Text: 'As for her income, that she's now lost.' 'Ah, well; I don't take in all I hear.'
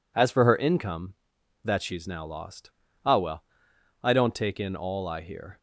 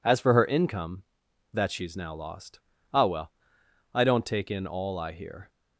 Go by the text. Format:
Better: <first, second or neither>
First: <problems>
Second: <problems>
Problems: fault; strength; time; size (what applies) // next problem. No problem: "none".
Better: neither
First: none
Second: none